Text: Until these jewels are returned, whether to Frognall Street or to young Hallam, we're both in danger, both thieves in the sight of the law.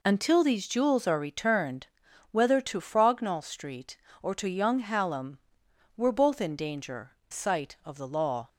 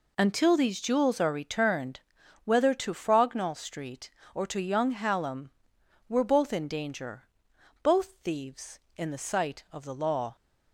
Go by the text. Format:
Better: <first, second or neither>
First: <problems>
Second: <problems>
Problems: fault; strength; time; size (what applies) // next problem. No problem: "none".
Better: second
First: skips "both thieves in the"; at 7.2 s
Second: none